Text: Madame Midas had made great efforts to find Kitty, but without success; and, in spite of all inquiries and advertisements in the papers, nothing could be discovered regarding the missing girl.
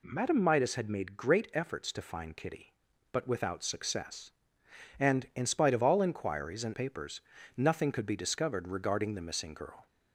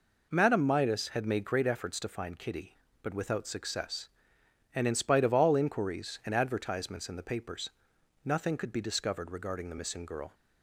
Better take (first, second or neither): second